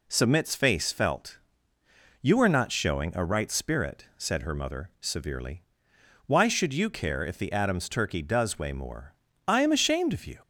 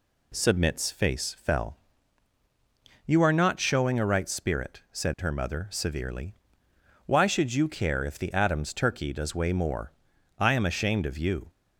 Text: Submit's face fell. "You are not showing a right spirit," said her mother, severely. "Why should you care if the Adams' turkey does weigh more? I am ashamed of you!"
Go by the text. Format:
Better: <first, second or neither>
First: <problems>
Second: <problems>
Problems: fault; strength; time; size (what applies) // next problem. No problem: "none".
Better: second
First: says "felt" for "fell"; at 0.9 s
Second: none